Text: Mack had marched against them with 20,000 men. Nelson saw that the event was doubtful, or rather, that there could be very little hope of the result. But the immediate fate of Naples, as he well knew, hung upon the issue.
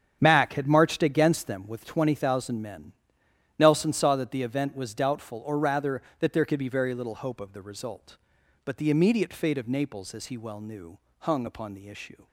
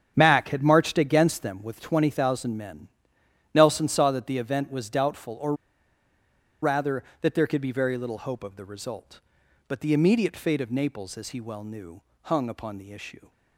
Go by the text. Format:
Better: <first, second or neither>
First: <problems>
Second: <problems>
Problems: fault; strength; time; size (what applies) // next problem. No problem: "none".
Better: first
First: starts louder than the rest; strong; until 1.2 s; 8.5 dB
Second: starts louder than the rest; strong; until 1.1 s; 8.5 dB // pauses between "or" and "rather"; at 5.5 s; 1.0 s long